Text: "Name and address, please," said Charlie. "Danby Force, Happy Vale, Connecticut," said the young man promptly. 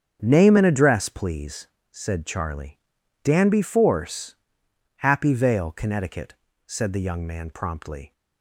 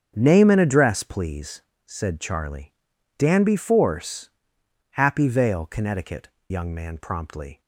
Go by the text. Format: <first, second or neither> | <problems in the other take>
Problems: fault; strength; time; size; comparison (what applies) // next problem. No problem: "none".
first | starts louder than the rest; strong; until 1.1 s; 7.5 dB; strong in the first // skips "said the"; at 6.3 s